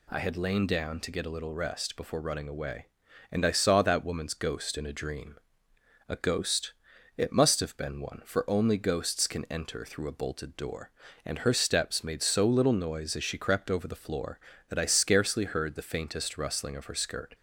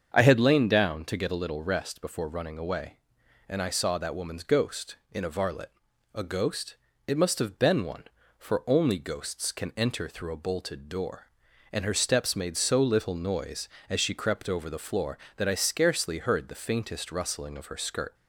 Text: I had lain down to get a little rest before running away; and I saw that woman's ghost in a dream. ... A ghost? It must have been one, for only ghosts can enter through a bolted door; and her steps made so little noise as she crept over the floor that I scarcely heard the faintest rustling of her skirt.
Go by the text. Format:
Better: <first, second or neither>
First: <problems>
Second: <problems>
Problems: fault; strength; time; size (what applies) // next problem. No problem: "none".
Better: first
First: none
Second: starts louder than the rest; until 1.1 s; 7 dB // says "varlet" for "dream"; at 5.2 s